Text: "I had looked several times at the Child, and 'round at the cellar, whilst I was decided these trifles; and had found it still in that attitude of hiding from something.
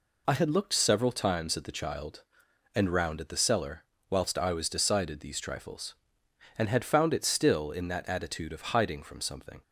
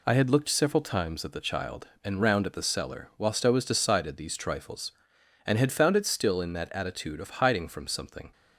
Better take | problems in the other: neither | none

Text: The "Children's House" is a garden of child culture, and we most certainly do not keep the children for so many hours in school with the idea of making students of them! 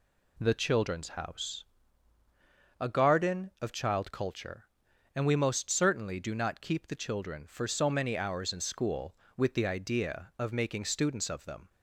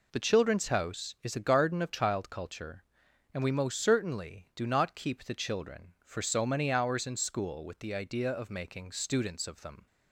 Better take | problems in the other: second | skips "is"; at 2.2 s

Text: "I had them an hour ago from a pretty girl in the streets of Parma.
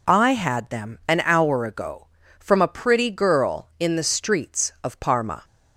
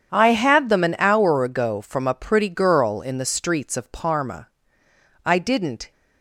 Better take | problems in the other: first | starts louder than the rest; strong; until 1.1 s; 8.5 dB // goes on to say "I didn't"; noticeable; from 5.2 s on; 0.66 s long

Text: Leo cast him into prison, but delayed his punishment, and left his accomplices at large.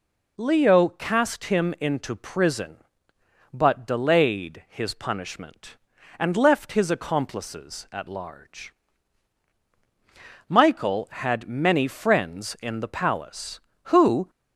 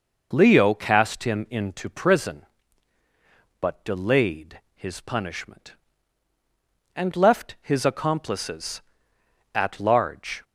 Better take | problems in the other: second | goes on to say "Michael had many friends in the palace who"; strong; from 10.4 s on; 3.8 s long

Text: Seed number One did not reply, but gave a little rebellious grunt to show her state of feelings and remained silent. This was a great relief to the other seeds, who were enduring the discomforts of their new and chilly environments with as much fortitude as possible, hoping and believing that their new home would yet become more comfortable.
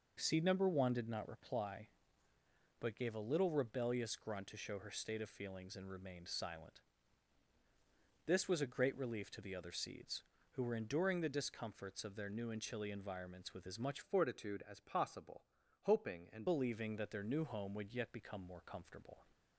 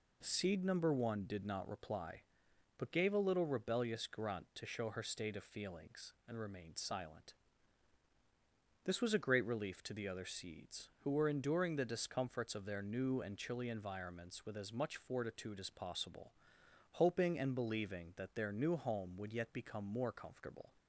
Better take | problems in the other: second | changes voice from "fortitude" to "and"; from 14.0 to 16.4 s; 2.4 s long

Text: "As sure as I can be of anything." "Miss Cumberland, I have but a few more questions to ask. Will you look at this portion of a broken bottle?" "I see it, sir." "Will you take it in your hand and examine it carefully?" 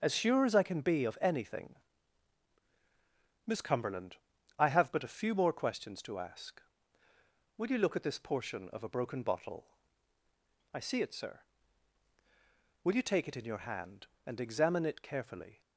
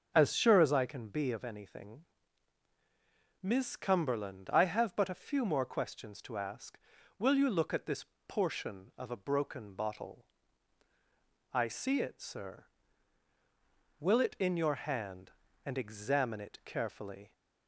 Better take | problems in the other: first | starts louder than the rest; until 1.1 s; 6 dB; noticeable in the first // pauses between "this" and "portion"; slight; at 8.0 s; 0.20 s long // skips "you take"; at 14.2 s

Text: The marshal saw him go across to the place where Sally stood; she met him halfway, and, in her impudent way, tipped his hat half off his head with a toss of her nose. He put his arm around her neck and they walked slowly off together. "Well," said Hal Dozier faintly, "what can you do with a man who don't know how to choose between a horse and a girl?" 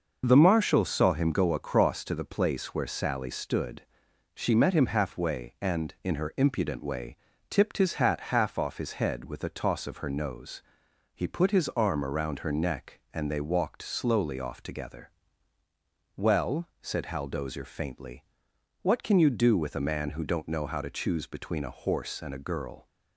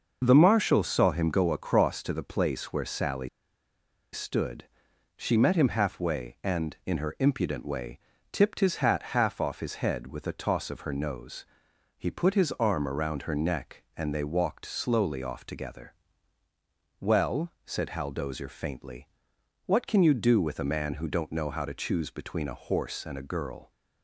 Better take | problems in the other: first | pauses between "Sally" and "stood"; noticeable; at 3.2 s; 0.86 s long

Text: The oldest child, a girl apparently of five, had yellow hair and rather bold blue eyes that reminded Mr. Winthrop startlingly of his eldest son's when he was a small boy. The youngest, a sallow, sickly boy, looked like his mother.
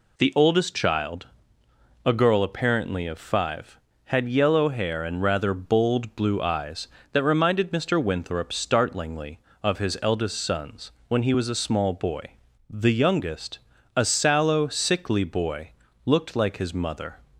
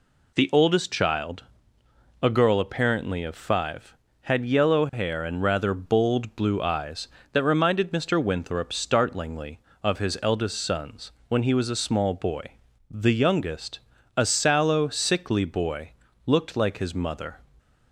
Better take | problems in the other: neither | pauses between "son's" and "when"; slight; the same in both

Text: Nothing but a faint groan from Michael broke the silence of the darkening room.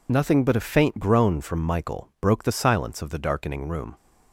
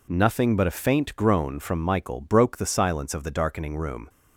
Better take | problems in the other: second | loses the start of "Nothing"; at 0.0 s; 35 ms

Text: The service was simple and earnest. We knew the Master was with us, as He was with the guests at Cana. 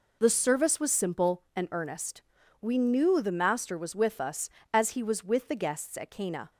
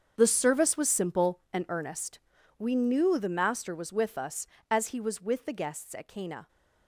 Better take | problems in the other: first | gets quieter; strong; throughout; 14.5 dB

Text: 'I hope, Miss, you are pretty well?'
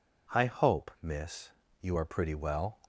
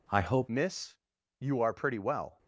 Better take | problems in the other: first | changes voice at "Miss"; from 0.4 s on; 1.9 s long

